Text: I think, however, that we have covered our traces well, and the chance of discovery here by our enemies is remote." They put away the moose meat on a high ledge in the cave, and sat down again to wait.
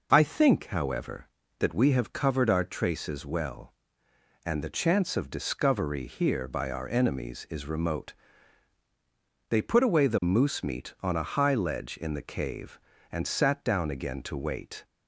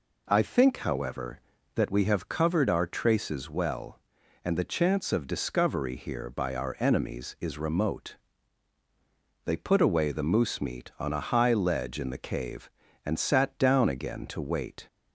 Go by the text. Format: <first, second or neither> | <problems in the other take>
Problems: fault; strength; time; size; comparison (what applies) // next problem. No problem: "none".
neither | none